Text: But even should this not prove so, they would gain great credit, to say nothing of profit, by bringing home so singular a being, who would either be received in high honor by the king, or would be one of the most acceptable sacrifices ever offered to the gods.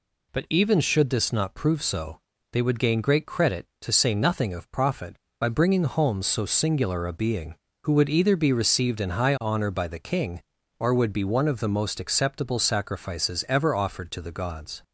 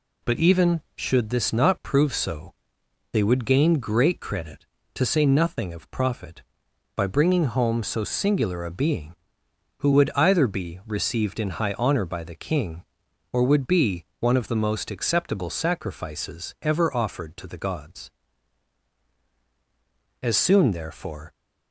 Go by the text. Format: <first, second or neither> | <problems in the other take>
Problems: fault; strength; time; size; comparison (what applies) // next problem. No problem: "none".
first | pauses between "be" and "one"; slight; at 14.0 s; 0.16 s long // goes on to say "As soon therefore"; noticeable; from 20.2 s on; 1.1 s long